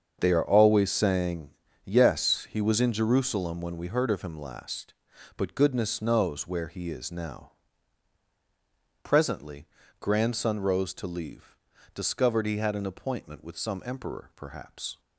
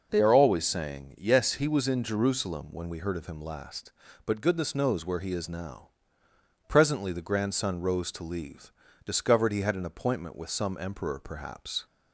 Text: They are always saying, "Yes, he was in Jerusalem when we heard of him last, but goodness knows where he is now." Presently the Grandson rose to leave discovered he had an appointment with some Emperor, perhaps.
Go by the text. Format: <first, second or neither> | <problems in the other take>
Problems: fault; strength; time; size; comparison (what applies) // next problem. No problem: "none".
second | starts louder than the rest; until 1.2 s; 7 dB // skips "the"; at 9.8 s // pauses between "leave" and "discovered"; at 11.5 s; 0.40 s long; slight in the second